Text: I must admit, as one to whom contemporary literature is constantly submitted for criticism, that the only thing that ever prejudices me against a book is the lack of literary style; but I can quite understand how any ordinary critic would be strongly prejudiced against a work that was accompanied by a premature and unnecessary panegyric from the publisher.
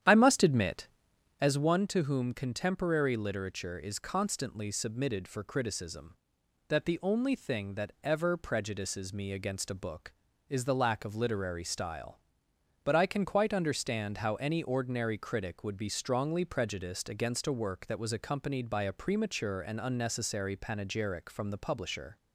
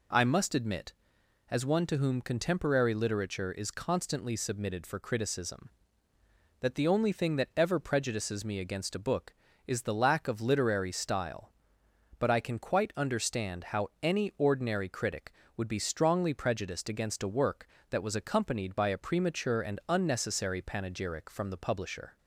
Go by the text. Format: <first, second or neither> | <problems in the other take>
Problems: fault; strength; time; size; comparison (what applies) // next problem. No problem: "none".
second | starts louder than the rest; strong; until 1.6 s; 10 dB